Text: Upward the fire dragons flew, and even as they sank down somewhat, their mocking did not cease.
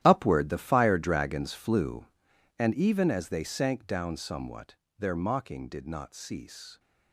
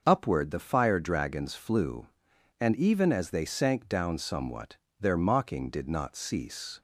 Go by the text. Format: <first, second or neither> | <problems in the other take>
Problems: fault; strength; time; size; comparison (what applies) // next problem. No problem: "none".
second | gets quieter; strong; throughout; 14.5 dB // starts louder than the rest; strong; until 1.0 s; 12 dB; also in the second